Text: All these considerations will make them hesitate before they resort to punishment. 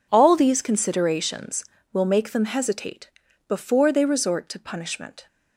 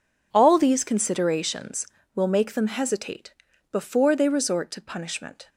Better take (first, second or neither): neither